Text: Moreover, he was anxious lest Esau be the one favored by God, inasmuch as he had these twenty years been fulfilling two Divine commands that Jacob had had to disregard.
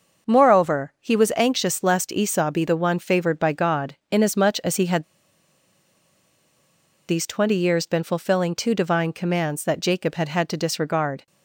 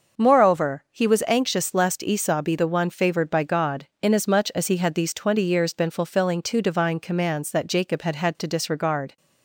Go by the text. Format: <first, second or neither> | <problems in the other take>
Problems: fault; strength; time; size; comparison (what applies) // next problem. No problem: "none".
second | pauses between "had" and "these"; strong; at 5.0 s; 2.0 s long